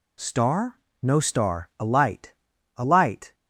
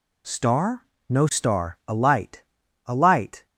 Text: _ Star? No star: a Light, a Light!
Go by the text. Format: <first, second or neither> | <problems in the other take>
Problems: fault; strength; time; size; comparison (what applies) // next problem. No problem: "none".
neither | none